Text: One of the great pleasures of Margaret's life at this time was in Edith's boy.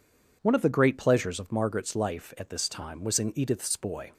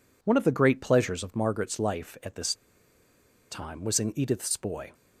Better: first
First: none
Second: pauses between "this" and "time"; noticeable; at 2.5 s; 0.97 s long

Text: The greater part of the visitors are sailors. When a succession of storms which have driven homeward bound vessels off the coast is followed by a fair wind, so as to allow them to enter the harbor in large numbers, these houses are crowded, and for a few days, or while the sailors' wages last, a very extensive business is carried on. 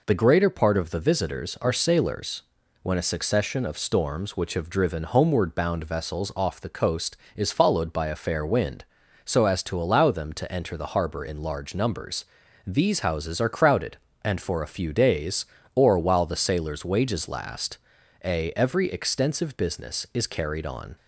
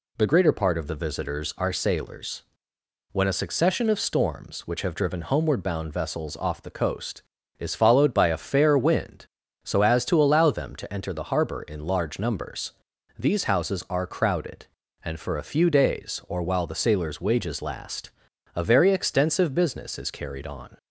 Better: second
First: says "every" for "very"; at 18.5 s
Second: none

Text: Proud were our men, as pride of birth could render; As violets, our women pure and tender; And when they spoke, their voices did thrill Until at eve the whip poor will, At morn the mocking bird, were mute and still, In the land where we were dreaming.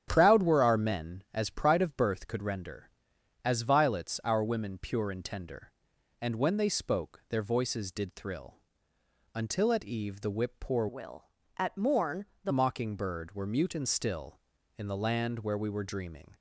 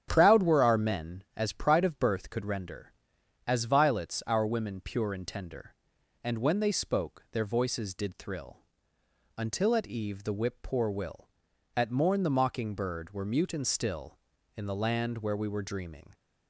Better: second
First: starts louder than the rest; strong; until 1.0 s; 9.5 dB // pauses between "thrill" and "Until"; noticeable; at 8.5 s; 0.80 s long // changes voice from "will" to "the"; from 10.8 to 12.5 s; 1.7 s long // pauses between "morn" and "the"; slight; at 12.2 s; 0.18 s long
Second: starts louder than the rest; strong; until 1.1 s; 9.5 dB // pauses between "thrill" and "Until"; noticeable; at 8.5 s; 0.80 s long

